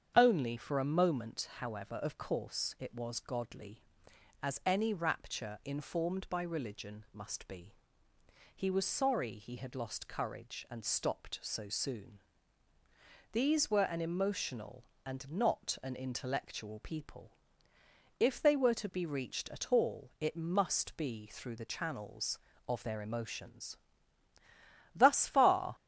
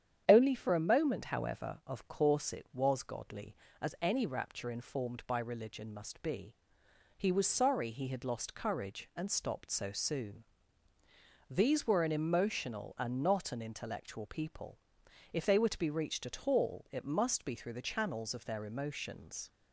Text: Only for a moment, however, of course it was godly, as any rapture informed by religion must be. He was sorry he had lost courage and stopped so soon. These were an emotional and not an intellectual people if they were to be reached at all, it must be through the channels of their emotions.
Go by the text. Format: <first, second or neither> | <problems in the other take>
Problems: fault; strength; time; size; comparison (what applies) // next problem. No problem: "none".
second | starts louder than the rest; strong; until 1.1 s; 8 dB; strong in the second // pauses between "people" and "if"; noticeable; at 17.3 s; 0.84 s long; noticeable in the second // goes on to say "Thus far"; noticeable; from 24.9 s on; 0.80 s long